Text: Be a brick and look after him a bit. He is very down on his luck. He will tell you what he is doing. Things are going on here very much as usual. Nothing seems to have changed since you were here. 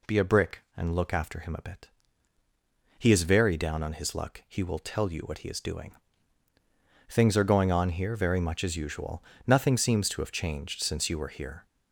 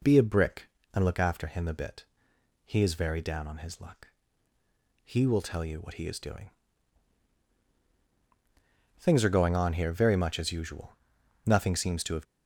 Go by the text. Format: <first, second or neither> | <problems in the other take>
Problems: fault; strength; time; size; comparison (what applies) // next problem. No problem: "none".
first | stops before "changed since you were here"; at 12.2 s